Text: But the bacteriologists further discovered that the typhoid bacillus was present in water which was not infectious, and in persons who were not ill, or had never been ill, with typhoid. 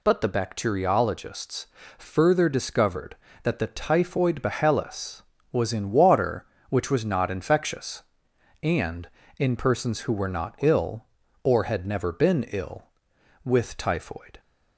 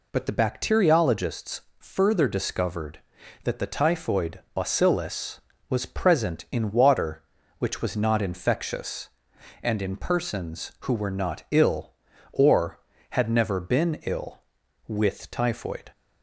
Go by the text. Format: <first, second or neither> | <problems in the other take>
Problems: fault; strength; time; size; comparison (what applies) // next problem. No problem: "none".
second | pauses between "bacteriologists" and "further"; slight; at 1.6 s; 0.30 s long; slight in the second // skips "present"; at 5.7 s